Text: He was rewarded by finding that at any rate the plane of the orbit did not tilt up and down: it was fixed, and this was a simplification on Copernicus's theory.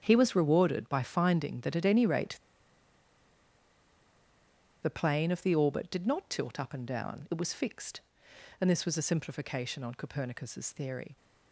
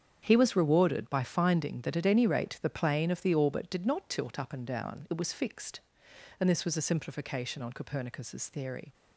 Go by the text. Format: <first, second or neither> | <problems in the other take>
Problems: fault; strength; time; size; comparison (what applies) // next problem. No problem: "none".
second | starts louder than the rest; strong; until 1.0 s; 8 dB; strong in the second // pauses between "rate" and "the"; strong; at 2.3 s; 2.4 s long